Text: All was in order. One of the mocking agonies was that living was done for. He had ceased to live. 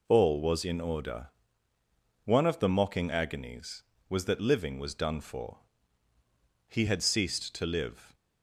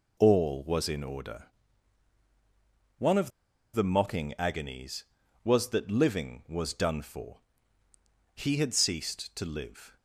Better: first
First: none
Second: pauses between "of" and "the"; at 3.3 s; 0.43 s long

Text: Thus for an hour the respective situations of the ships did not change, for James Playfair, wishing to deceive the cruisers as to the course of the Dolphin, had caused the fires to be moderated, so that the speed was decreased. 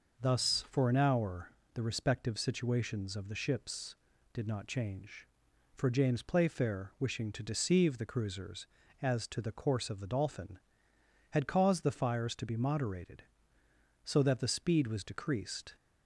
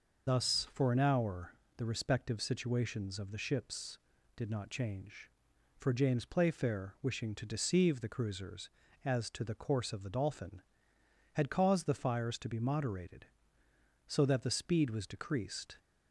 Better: first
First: pauses between "hour" and "the"; slight; at 1.5 s; 0.24 s long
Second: loses the start of "Thus"; at 0.2 s; 45 ms // pauses between "hour" and "the"; slight; at 1.5 s; 0.24 s long

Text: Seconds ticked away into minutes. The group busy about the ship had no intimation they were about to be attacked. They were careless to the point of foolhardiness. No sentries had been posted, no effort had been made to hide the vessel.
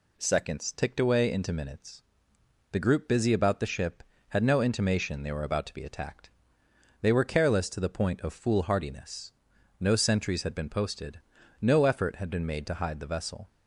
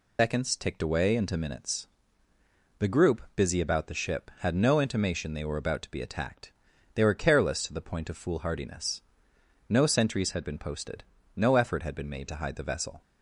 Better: first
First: none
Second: loses the start of "Seconds"; at 0.1 s; 130 ms

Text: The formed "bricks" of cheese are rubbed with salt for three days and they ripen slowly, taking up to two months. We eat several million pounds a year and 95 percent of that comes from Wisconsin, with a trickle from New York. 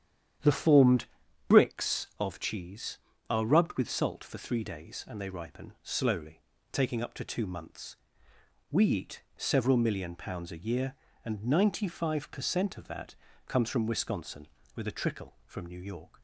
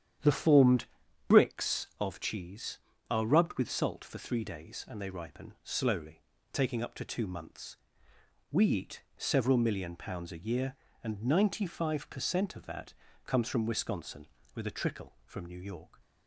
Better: neither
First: starts louder than the rest; strong; until 1.8 s; 9.5 dB // pauses between "formed" and "bricks"; noticeable; at 1.0 s; 0.46 s long // pauses between "that" and "comes"; slight; at 13.1 s; 0.32 s long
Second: starts louder than the rest; strong; until 1.6 s; 9.5 dB // pauses between "formed" and "bricks"; noticeable; at 0.8 s; 0.46 s long // pauses between "that" and "comes"; slight; at 12.9 s; 0.32 s long

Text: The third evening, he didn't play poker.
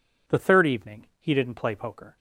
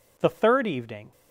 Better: first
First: none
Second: stops before "he didn't play poker"; at 1.1 s

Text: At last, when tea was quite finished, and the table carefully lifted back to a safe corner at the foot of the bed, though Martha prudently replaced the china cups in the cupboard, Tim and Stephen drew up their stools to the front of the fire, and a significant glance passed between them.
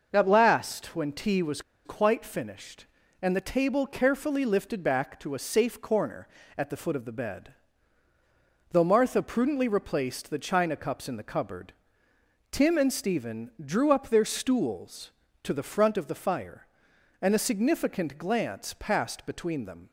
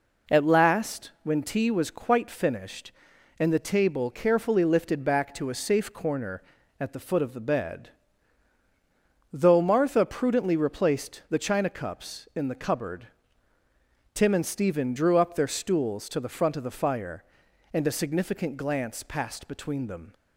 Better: second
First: pauses between "was" and "quite"; slight; at 1.6 s; 0.23 s long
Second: none

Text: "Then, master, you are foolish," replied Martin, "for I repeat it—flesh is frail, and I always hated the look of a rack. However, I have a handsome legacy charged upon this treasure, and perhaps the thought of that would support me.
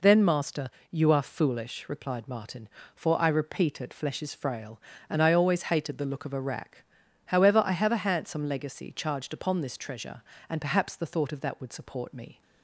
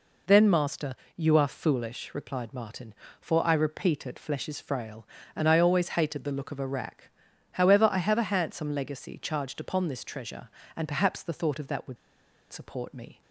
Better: first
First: none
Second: pauses between "would" and "support"; noticeable; at 11.9 s; 0.54 s long

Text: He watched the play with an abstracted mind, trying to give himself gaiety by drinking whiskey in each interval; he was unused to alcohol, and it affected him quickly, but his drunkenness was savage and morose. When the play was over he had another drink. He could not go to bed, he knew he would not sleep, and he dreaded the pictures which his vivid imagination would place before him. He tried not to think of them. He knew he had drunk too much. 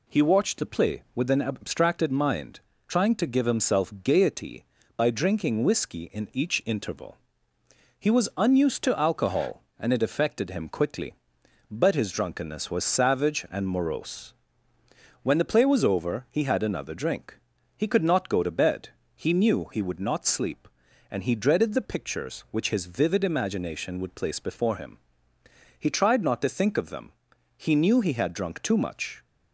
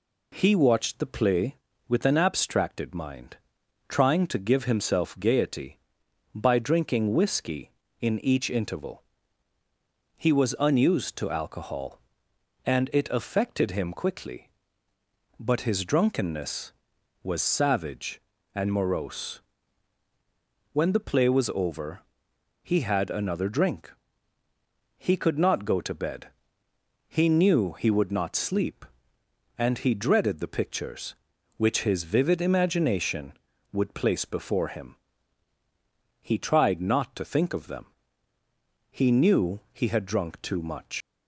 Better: first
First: none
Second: pauses between "over" and "he"; noticeable; at 21.9 s; 0.64 s long // leaves "much" unfinished; at 41.0 s; 125 ms

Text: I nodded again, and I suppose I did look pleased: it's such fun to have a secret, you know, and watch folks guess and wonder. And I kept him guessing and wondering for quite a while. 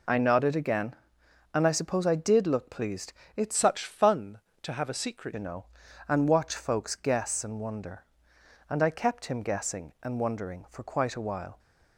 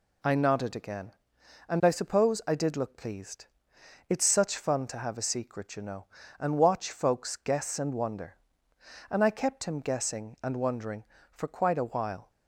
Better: second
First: changes voice from "such" to "secret"; from 3.5 to 5.3 s; 1.8 s long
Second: none

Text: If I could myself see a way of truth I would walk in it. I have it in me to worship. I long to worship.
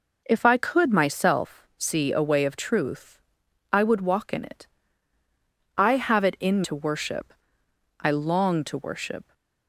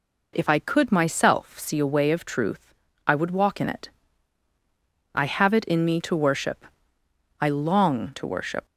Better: second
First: pauses between "truth" and "I"; noticeable; at 3.1 s; 0.54 s long // skips "me"; at 6.6 s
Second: pauses between "truth" and "I"; slight; at 2.7 s; 0.32 s long

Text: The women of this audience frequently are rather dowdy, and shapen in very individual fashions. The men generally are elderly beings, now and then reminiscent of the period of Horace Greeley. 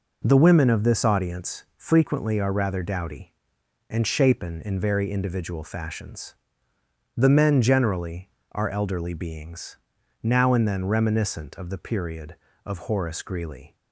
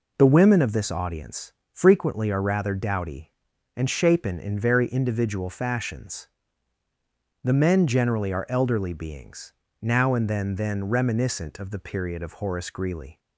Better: first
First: none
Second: pauses between "audience" and "frequently"; slight; at 1.5 s; 0.22 s long // says "then" twice; at 10.5 s

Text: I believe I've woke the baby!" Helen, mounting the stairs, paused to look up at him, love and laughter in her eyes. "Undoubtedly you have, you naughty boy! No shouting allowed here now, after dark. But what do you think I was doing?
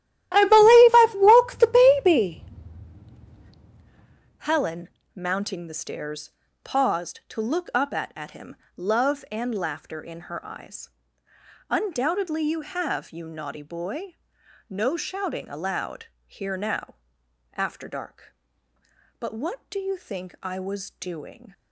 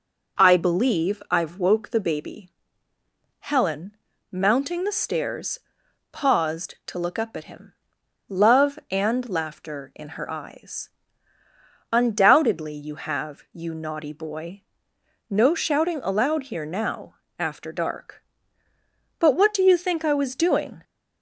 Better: second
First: starts louder than the rest; strong; until 1.3 s; 13.5 dB // says "at" twice; at 8.1 s // pauses between "allowed" and "here"; slight; at 16.0 s; 0.18 s long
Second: none

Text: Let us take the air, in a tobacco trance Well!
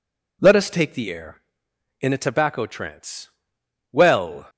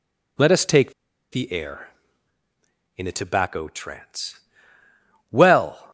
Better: first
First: pauses between "trance" and "Well"; noticeable; at 3.2 s; 0.61 s long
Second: pauses between "take" and "the"; at 0.9 s; 0.40 s long // pauses between "trance" and "Well"; noticeable; at 4.3 s; 0.90 s long

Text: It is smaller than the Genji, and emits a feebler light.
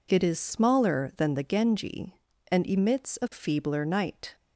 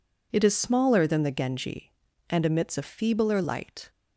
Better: second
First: says "night" for "light"; at 3.8 s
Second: none

